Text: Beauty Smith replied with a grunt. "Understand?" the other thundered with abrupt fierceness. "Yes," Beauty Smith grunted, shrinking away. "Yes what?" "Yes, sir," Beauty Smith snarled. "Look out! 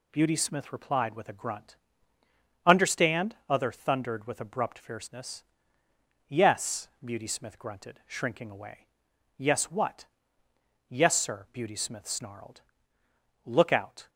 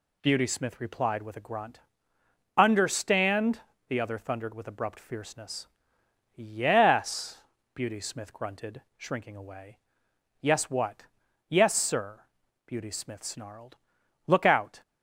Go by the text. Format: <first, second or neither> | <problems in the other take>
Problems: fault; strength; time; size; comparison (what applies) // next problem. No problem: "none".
second | skips "the"; at 3.4 s